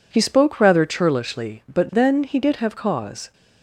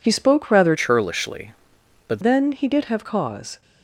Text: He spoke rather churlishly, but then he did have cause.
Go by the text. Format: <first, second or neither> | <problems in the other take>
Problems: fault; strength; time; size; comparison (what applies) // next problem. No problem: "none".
first | changes voice from "churlishly" to "but"; from 0.7 to 2.2 s; 1.5 s long